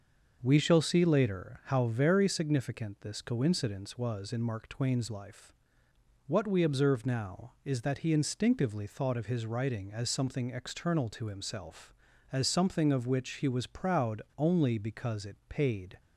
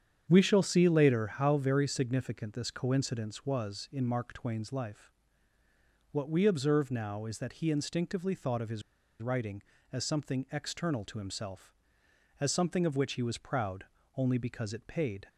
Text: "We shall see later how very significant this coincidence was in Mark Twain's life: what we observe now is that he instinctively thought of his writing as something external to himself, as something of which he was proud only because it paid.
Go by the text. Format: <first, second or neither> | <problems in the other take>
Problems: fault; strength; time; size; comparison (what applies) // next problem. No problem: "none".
first | starts louder than the rest; strong; until 1.3 s; 8 dB; noticeable in the first // pauses between "his" and "writing"; at 8.8 s; 0.40 s long // pauses between "proud" and "only"; slight; at 13.8 s; 0.32 s long